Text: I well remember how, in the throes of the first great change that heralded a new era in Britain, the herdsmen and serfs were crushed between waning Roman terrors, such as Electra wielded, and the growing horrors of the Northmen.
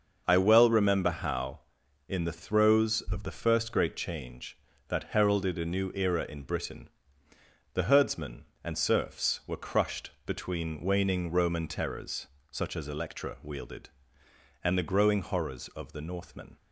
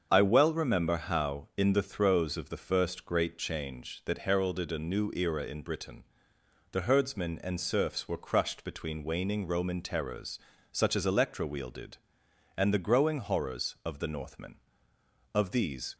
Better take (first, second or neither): first